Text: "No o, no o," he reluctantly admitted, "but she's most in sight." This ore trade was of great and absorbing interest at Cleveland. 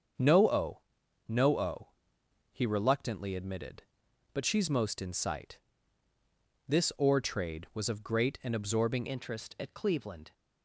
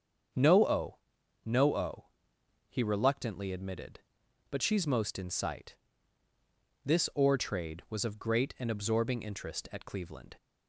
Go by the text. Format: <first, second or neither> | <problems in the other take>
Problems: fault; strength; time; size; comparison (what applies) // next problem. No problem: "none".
second | starts louder than the rest; until 1.6 s; 7 dB; strong in the second // changes voice at "interest"; from 9.0 s on; 1.3 s long